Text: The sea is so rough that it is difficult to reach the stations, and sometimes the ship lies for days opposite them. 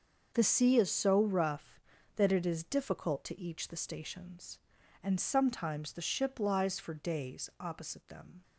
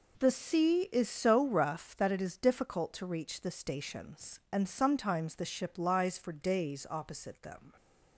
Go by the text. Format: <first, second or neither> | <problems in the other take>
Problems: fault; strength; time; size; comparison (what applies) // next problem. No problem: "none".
second | starts louder than the rest; until 1.3 s; 6 dB // says "each" for "reach"; at 3.3 s